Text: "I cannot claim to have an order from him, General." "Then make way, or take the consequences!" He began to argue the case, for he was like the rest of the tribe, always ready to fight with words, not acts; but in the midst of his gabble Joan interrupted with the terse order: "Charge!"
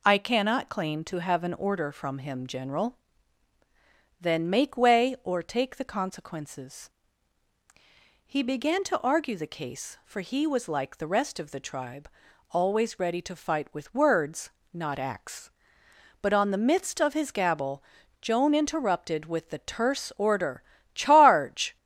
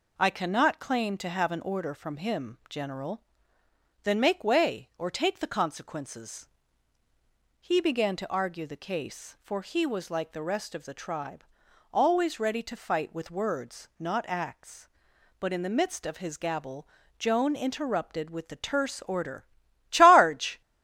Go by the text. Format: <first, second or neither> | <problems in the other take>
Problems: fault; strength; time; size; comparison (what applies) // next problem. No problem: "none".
second | says "on" for "in"; at 16.3 s // pauses between "gabble" and "Joan"; at 17.8 s; 0.38 s long; slight in the second